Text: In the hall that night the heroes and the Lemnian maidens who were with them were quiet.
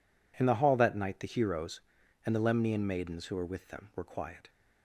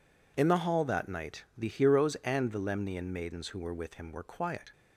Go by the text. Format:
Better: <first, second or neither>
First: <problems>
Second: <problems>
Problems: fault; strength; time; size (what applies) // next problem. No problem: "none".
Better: first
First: none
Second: says "him" for "them"; at 3.9 s